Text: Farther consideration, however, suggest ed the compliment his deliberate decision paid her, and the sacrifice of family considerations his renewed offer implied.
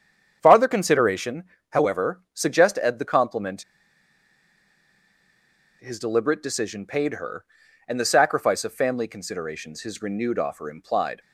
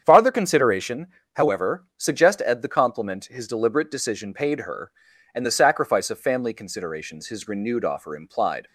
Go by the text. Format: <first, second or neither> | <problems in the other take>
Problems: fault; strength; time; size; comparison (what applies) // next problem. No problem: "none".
second | starts louder than the rest; strong; until 1.4 s; 8 dB; strong in the second // pauses between "compliment" and "his"; strong; at 3.6 s; 2.1 s long